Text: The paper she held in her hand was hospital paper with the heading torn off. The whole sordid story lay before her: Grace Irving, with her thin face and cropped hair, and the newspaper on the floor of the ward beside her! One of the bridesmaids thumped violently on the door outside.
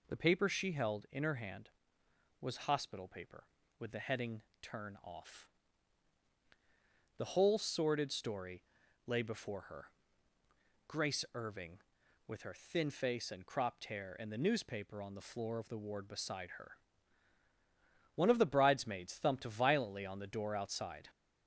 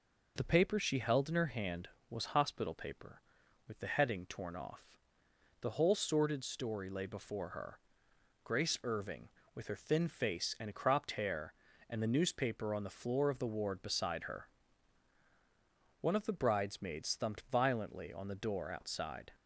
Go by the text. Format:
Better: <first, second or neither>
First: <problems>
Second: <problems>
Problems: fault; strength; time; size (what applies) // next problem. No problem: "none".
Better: second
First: says "turn" for "torn"; at 4.6 s // pauses between "story" and "lay"; at 8.6 s; 0.44 s long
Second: none